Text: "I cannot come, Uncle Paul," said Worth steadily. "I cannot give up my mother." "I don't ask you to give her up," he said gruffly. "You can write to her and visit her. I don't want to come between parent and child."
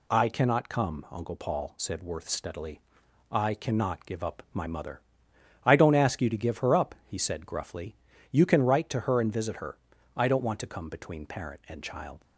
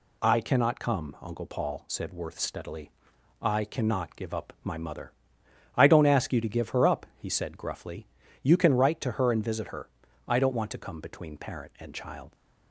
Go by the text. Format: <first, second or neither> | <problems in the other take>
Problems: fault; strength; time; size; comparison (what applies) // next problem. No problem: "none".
neither | none